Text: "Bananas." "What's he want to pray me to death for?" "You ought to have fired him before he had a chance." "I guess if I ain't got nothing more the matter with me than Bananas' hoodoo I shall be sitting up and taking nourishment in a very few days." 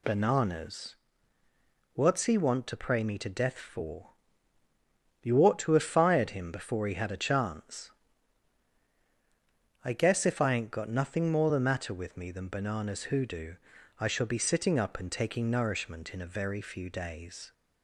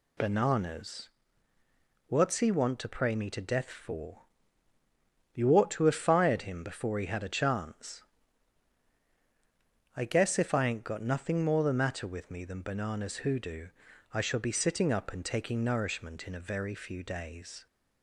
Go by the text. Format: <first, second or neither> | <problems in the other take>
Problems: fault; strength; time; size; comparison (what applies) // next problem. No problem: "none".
neither | pauses between "hoodoo" and "I"; the same in both